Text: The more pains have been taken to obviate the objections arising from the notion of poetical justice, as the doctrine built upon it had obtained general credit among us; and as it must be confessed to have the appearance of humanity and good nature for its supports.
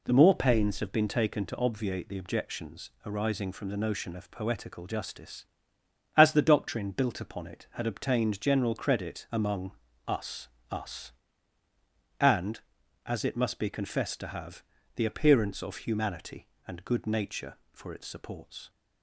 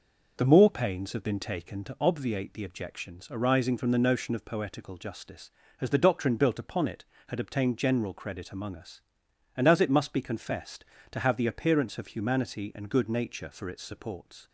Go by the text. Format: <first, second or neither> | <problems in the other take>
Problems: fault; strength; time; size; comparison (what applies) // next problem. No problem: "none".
second | pauses between "objections" and "arising"; slight; at 2.8 s; 0.16 s long // pauses between "among" and "us"; slight; at 9.7 s; 0.36 s long // says "us" twice; at 10.7 s // pauses between "have" and "the"; slight; at 14.6 s; 0.34 s long